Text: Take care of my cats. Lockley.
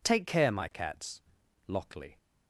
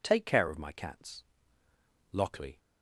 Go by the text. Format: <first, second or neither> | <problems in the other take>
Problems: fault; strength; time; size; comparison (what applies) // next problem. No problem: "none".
second | skips "of"; at 0.5 s